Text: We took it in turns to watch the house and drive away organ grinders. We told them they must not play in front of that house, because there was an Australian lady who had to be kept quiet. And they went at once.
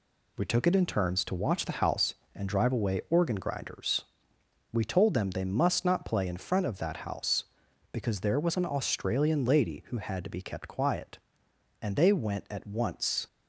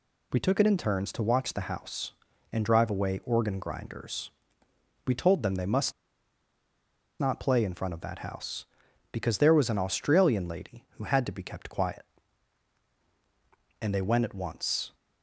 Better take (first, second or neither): first